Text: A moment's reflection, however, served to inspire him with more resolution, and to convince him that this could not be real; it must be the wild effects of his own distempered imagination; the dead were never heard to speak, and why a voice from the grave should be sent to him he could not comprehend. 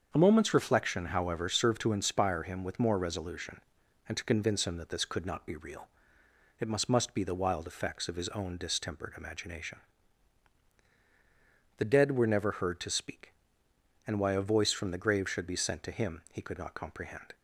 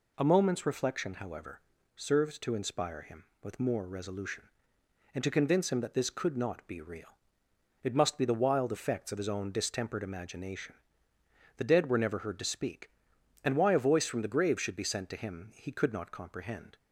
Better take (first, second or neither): second